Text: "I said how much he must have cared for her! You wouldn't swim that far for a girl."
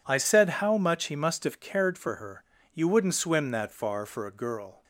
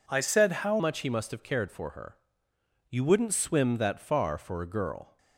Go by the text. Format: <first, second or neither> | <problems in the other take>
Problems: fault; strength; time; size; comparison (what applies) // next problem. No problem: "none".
first | changes voice at "much"; from 0.7 s on; 4.4 s long